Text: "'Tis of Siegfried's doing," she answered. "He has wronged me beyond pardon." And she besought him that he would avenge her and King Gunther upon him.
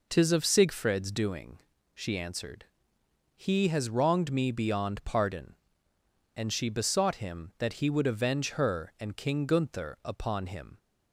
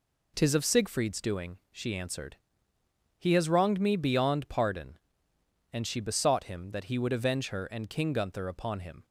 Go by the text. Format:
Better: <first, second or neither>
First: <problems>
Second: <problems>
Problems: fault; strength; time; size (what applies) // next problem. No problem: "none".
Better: neither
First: none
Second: none